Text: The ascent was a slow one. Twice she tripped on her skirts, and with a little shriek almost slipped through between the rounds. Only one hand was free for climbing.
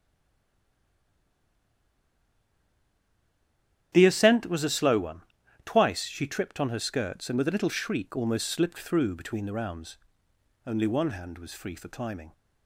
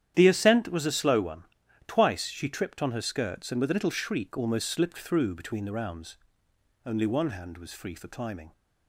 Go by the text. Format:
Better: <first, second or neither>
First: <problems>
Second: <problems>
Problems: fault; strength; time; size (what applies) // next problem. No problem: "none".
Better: second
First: stays silent before the first word; strong; until 3.9 s; 3.9 s long // starts louder than the rest; strong; until 4.9 s; 10.5 dB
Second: starts louder than the rest; strong; until 1.1 s; 10.5 dB